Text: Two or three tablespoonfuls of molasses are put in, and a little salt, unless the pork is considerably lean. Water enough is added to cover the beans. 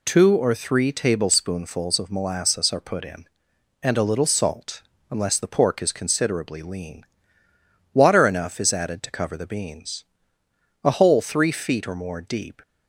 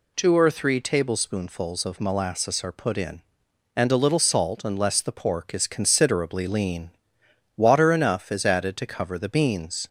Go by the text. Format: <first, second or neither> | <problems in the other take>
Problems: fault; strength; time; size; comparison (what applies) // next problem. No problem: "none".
second | goes on to say "A hole three feet or more deep"; strong; from 10.8 s on; 1.7 s long